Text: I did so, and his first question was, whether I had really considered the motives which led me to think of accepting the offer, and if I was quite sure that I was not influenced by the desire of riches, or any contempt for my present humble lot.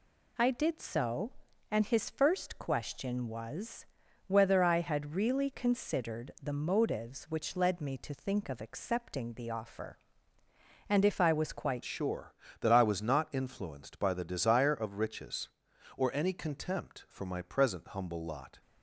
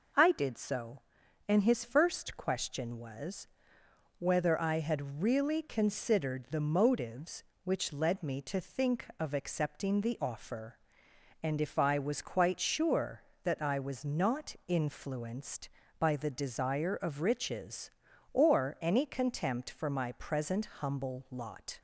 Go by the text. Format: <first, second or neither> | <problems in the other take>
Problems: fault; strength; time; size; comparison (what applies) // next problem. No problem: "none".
second | changes voice at "sure"; from 11.8 s on; 6.8 s long